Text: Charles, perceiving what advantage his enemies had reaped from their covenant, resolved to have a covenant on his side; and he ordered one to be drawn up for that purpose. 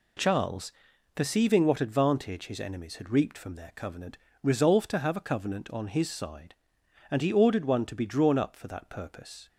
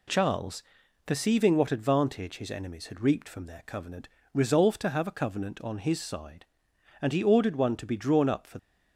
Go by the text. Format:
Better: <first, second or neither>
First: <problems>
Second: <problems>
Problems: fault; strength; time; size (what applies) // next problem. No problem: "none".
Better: first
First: none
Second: stops before "that purpose"; at 8.5 s